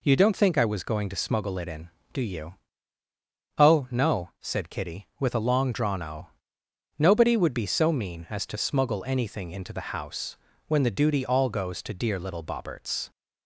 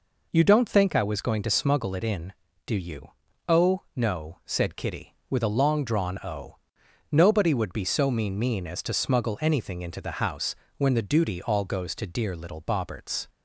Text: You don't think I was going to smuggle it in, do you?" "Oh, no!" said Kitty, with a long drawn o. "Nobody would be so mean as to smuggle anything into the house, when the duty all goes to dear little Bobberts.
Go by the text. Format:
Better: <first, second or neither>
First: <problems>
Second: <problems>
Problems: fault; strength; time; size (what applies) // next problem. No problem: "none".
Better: first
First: none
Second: says "mean" twice; at 8.3 s